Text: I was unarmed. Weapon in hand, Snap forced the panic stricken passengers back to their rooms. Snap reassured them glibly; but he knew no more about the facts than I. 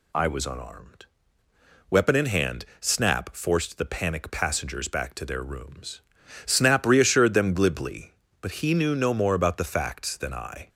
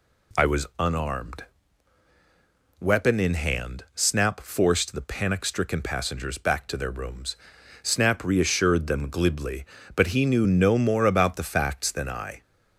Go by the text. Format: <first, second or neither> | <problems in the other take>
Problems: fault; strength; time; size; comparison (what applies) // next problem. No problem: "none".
second | skips "stricken"; at 4.3 s